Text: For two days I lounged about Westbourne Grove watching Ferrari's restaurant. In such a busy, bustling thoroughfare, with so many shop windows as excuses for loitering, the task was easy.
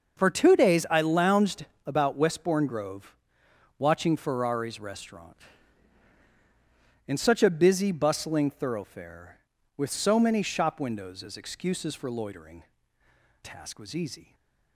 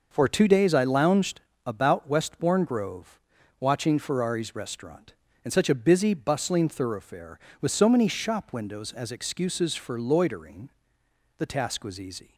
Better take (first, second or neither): second